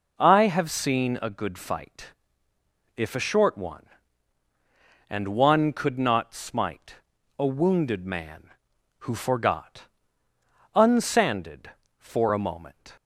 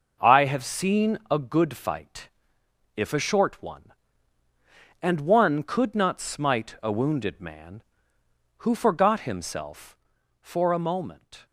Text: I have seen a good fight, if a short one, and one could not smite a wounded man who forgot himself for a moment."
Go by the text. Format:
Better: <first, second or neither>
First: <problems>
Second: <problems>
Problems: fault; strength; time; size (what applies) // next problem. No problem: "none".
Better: second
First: pauses between "smite" and "a"; at 6.9 s; 0.42 s long // says "unsanded" for "himself"; at 10.7 s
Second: none